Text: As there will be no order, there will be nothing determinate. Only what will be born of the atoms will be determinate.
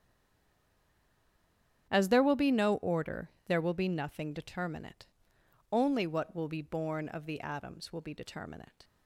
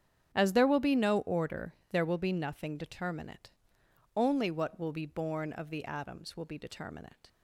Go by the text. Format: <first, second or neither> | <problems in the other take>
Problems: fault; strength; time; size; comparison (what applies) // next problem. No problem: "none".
second | stays silent before the first word; noticeable; until 1.8 s; 1.8 s long // starts louder than the rest; strong; until 2.9 s; 8.5 dB; strong in the second